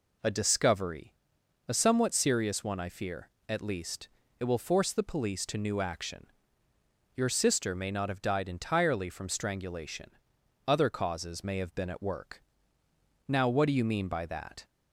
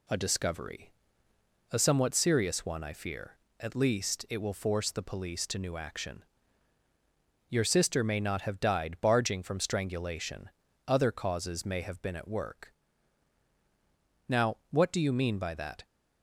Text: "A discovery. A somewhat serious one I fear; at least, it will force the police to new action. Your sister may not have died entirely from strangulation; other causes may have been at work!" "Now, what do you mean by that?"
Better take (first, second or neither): first